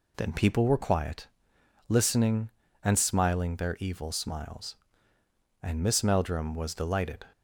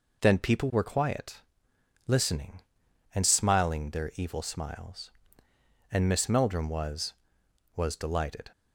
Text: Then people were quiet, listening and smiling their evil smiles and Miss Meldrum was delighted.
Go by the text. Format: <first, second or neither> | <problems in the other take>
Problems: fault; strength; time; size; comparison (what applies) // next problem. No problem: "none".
first | says "was" twice; at 7.7 s